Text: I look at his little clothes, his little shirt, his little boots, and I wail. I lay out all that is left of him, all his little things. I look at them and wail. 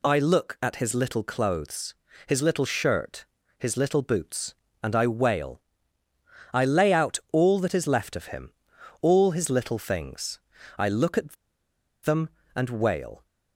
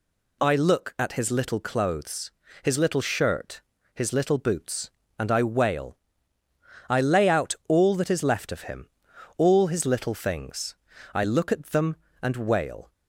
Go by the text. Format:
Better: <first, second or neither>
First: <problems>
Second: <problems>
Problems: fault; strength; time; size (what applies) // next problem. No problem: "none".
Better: second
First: pauses between "at" and "them"; noticeable; at 11.3 s; 0.69 s long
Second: none